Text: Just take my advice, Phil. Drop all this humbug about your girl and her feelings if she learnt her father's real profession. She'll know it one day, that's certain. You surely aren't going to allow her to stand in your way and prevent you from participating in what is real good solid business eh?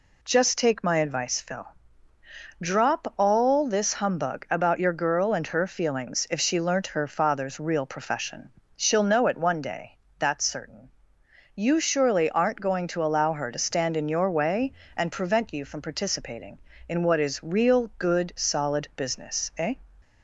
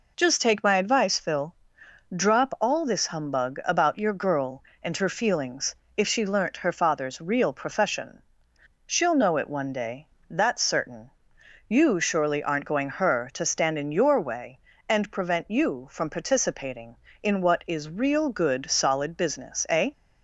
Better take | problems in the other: first | pauses between "feelings" and "if"; slight; at 5.7 s; 0.24 s long // skips "to allow"; at 12.9 s

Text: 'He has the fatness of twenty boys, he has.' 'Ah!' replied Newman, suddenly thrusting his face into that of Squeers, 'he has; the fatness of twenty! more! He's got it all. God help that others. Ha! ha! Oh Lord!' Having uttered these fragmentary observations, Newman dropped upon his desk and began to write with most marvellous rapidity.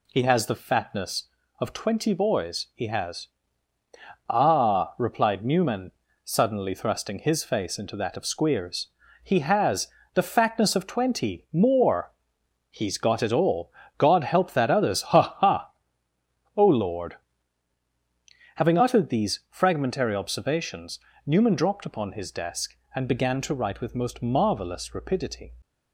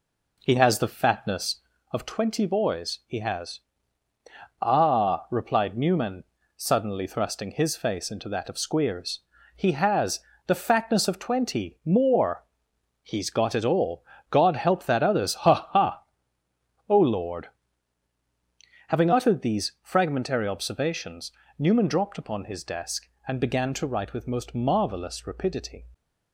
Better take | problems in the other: first | starts louder than the rest; slight; until 2.0 s; 3 dB

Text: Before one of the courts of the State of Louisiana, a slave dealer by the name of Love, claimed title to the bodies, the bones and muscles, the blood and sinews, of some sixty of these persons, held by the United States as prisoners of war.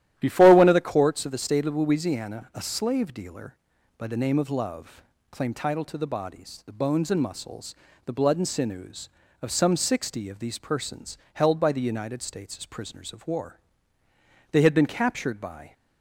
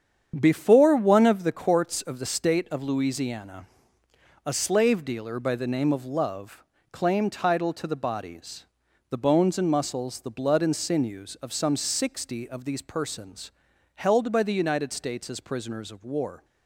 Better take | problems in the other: second | starts louder than the rest; strong; until 1.1 s; 12 dB; strong in the second // goes on to say "They had been captured by"; noticeable; from 14.5 s on; 1.2 s long

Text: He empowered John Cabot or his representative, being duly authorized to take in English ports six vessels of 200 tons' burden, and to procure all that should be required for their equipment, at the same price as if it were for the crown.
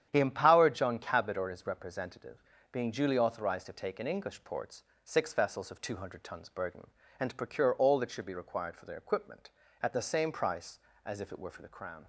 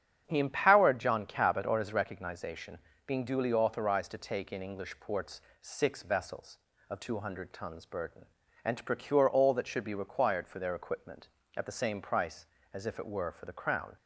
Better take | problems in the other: first | starts louder than the rest; strong; until 1.2 s; 8.5 dB; strong in the first // says "recognization" for "representative"; at 1.9 s // pauses between "ports" and "six"; slight; at 5.4 s; 0.20 s long; slight in the first

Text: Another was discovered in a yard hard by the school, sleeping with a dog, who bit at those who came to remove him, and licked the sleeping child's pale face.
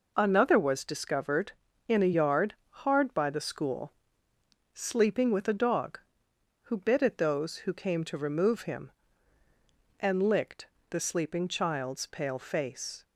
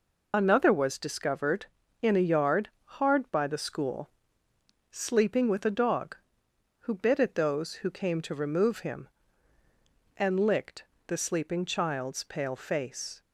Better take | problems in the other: first | loses the start of "Another"; at 0.3 s; 45 ms // pauses between "yard" and "hard"; slight; at 2.6 s; 0.16 s long; slight in the first // pauses between "licked" and "the"; slight; at 10.8 s; 0.24 s long; slight in the first

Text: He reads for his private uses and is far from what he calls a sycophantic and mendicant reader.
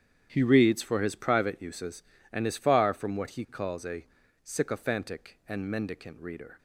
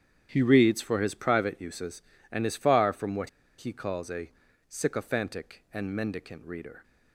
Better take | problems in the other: first | starts louder than the rest; strong; until 1.3 s; 8.5 dB; strong in the first // pauses between "what" and "he"; slight; at 3.2 s; 0.29 s long // pauses between "a" and "sycophantic"; slight; at 4.3 s; 0.36 s long; slight in the first

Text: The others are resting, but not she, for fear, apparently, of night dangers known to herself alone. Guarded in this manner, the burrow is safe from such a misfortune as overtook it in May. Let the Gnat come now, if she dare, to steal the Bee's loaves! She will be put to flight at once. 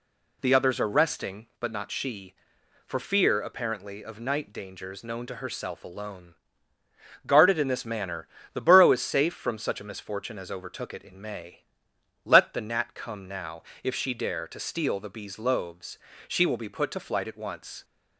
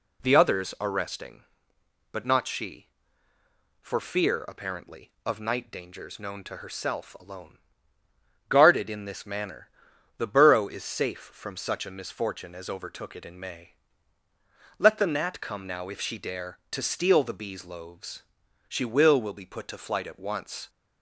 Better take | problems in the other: first | says "will" twice; at 19.1 s

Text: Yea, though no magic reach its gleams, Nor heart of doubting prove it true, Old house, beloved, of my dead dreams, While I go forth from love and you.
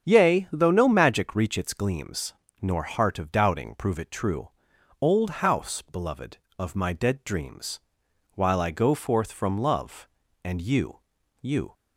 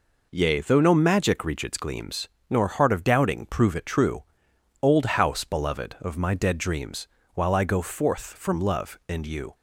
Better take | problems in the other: second | starts louder than the rest; strong; until 1.0 s; 7.5 dB // says "you" twice; at 11.4 s

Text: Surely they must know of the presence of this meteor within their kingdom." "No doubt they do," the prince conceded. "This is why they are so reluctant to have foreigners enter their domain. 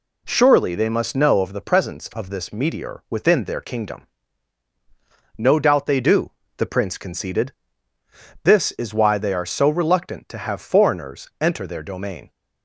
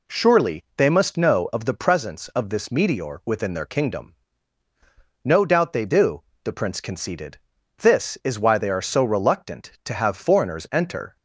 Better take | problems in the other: first | stops before "their domain"; at 11.1 s

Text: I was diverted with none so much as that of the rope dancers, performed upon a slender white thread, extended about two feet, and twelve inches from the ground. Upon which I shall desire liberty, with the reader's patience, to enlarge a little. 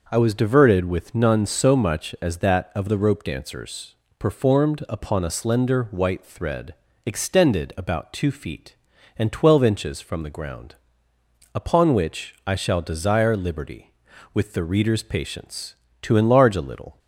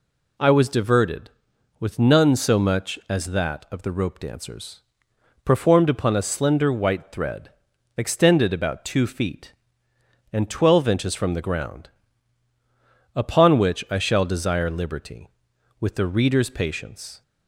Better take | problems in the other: first | stops before "to enlarge a little"; at 17.2 s

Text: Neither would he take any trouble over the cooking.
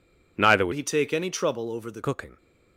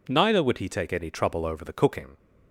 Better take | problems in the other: second | changes voice from "he" to "the"; from 0.7 to 2.0 s; 1.3 s long

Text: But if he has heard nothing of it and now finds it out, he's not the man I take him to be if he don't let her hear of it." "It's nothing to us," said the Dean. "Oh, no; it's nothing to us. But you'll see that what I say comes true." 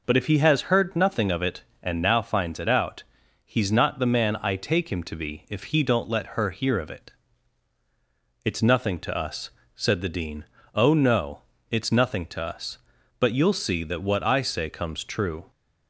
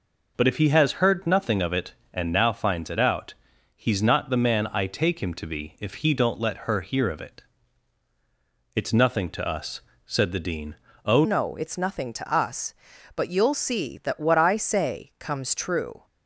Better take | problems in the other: first | changes voice at "no"; from 11.2 s on; 4.8 s long

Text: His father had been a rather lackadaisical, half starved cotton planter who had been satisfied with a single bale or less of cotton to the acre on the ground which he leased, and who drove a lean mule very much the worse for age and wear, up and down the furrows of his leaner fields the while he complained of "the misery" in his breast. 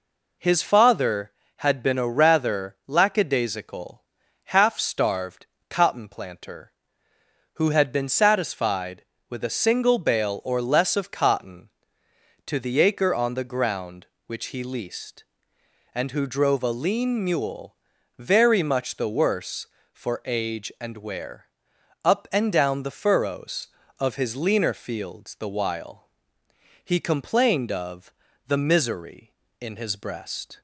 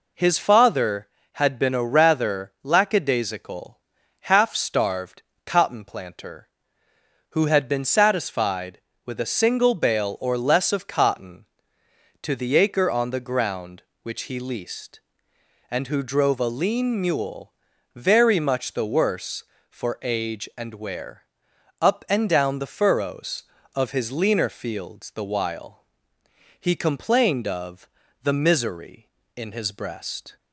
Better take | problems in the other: neither | pauses between "starved" and "cotton"; slight; the same in both // pauses between "mule" and "very"; the same in both // pauses between "while" and "he"; noticeable; the same in both // pauses between "of" and "the"; slight; the same in both

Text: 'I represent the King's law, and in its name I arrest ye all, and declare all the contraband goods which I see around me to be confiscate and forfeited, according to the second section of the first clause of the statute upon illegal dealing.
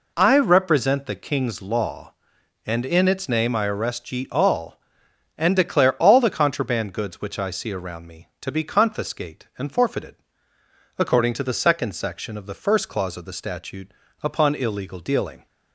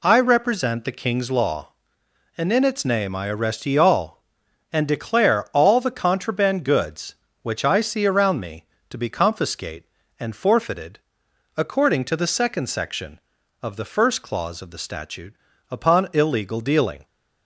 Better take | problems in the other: neither | pauses between "statute" and "upon"; slight; the same in both

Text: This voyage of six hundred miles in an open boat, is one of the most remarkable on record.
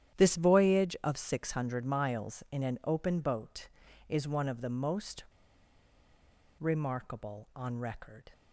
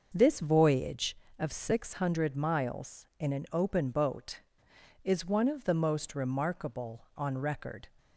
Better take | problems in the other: second | starts louder than the rest; strong; until 1.2 s; 10.5 dB; noticeable in the second // pauses between "most" and "remarkable"; strong; at 5.2 s; 1.3 s long

